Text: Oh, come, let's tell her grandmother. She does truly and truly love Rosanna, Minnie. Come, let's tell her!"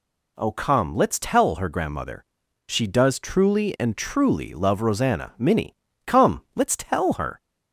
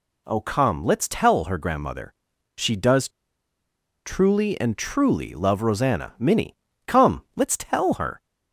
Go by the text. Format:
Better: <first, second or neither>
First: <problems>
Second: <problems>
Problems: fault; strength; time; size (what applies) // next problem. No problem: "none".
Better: first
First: none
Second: pauses between "does" and "truly"; noticeable; at 3.0 s; 0.96 s long